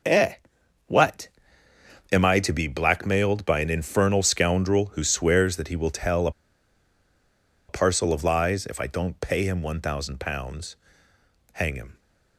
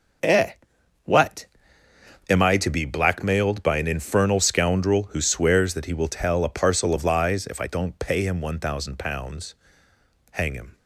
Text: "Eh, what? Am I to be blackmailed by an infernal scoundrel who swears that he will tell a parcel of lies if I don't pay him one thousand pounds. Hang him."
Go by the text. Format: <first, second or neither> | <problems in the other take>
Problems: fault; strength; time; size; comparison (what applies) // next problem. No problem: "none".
second | starts louder than the rest; until 2.3 s; 6 dB; noticeable in the second // pauses between "a" and "parcel"; strong; at 6.3 s; 1.3 s long